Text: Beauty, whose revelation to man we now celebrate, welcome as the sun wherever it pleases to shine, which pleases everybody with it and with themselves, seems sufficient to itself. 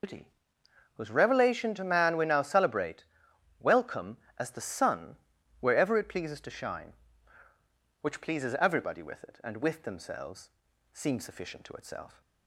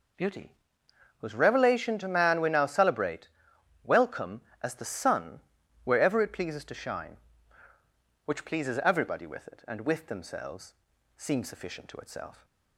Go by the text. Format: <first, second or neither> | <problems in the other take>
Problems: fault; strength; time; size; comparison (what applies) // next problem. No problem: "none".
second | loses the start of "Beauty"; at 0.0 s; 110 ms // pauses between "sun" and "wherever"; at 5.1 s; 0.44 s long; also in the second